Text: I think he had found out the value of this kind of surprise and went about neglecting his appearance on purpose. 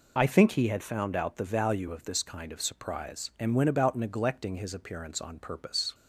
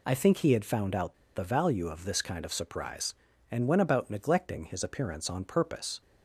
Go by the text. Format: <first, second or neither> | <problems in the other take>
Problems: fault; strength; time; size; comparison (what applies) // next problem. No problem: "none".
first | pauses between "out" and "the"; slight; at 1.1 s; 0.21 s long